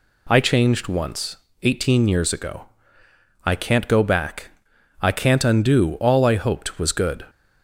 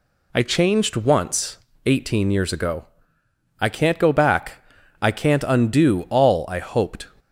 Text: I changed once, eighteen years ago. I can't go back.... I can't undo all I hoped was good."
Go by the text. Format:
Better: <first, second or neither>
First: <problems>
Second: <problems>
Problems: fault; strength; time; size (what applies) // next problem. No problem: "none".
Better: first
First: none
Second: stops before "was good"; at 7.1 s